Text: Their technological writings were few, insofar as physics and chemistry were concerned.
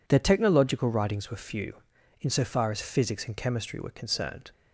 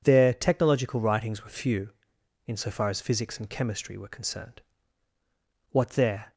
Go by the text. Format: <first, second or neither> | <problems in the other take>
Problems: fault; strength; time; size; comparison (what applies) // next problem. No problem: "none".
first | goes on to say "What there"; noticeable; from 5.7 s on; 0.62 s long